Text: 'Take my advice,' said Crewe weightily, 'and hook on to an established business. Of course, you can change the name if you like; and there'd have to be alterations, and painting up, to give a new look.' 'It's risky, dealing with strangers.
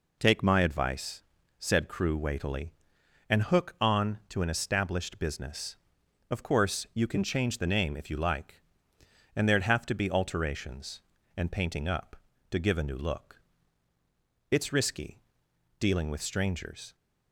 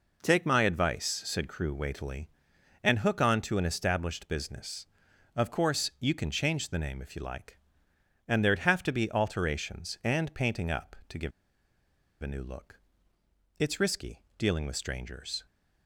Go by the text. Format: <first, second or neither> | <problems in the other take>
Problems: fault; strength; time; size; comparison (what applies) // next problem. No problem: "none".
first | pauses between "give" and "a"; noticeable; at 11.3 s; 0.90 s long